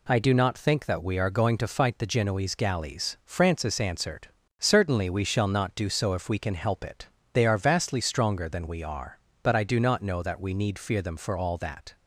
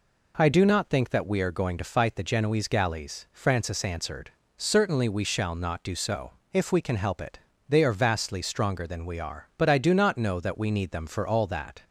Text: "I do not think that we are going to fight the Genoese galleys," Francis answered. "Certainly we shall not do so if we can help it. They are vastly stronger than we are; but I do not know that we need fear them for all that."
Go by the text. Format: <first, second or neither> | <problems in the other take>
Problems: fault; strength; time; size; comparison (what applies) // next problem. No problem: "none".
first | pauses between "so" and "if"; slight; at 6.3 s; 0.18 s long // skips "fear"; at 10.8 s